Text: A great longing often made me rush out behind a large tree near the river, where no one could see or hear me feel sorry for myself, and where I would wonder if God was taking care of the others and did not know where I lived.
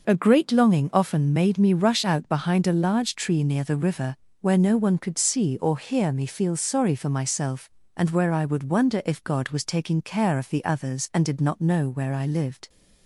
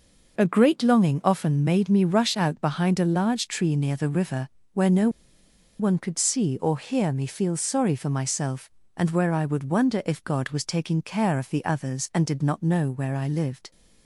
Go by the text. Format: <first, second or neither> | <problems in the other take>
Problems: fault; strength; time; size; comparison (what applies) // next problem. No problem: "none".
first | pauses between "no" and "one"; noticeable; at 5.0 s; 0.70 s long